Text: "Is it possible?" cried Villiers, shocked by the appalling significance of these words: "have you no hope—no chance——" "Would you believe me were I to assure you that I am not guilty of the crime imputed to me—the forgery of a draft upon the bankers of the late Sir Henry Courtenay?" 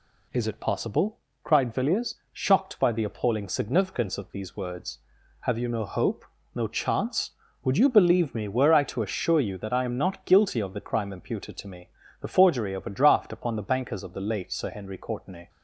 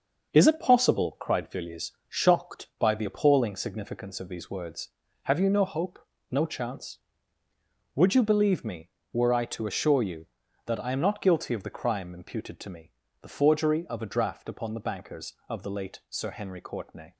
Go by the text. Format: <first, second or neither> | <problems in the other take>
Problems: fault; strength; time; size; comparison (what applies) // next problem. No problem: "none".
first | gets quieter; throughout; 6.5 dB